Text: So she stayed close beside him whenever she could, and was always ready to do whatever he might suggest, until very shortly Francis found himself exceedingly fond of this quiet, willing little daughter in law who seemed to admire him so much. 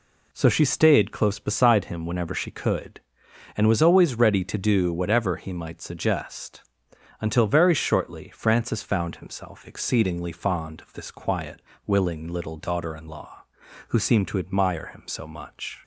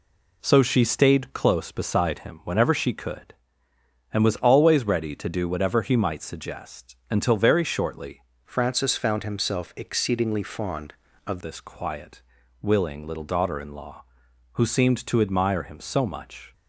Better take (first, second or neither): first